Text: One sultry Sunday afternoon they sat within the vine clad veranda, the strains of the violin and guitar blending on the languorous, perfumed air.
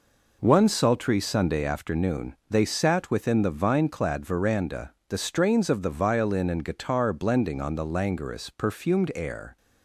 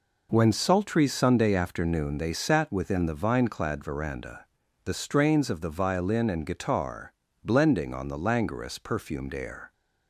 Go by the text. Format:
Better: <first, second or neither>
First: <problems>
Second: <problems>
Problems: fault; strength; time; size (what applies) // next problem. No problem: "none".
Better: first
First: none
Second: says "When" for "One"; at 0.3 s // pauses between "guitar" and "blending"; slight; at 7.1 s; 0.30 s long